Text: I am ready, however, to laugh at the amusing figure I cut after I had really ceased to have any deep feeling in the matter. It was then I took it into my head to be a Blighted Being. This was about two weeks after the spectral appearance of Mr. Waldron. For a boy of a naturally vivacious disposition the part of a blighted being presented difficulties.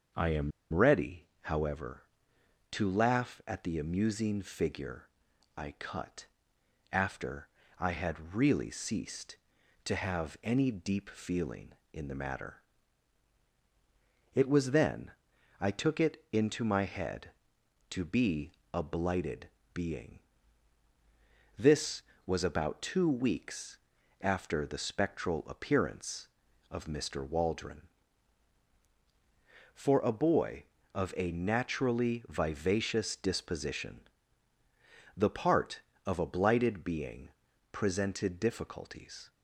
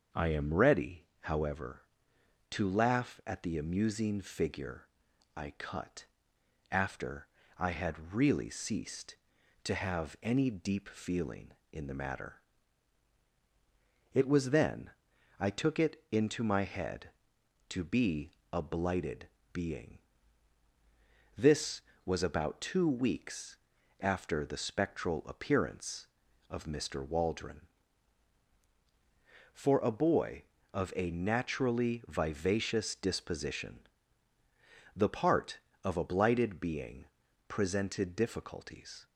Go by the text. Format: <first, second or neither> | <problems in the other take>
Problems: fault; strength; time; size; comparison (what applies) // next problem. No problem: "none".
second | starts louder than the rest; until 1.5 s; 6.5 dB; also in the second // pauses between "am" and "ready"; slight; at 0.5 s; 0.21 s long // pauses between "figure" and "I"; noticeable; at 5.0 s; 0.50 s long; noticeable in the second // pauses between "cut" and "after"; noticeable; at 6.2 s; 0.66 s long; noticeable in the second // pauses between "after" and "I"; slight; at 7.4 s; 0.30 s long; slight in the second // pauses between "then" and "I"; noticeable; at 15.1 s; 0.50 s long; noticeable in the second // pauses between "be" and "a"; slight; at 18.5 s; 0.20 s long; slight in the second // pauses between "Blighted" and "Being"; slight; at 19.4 s; 0.26 s long; slight in the second // pauses between "weeks" and "after"; noticeable; at 23.7 s; 0.46 s long; noticeable in the second // pauses between "disposition" and "the"; at 34.0 s; 1.1 s long; also in the second // pauses between "being" and "presented"; at 37.2 s; 0.44 s long; also in the second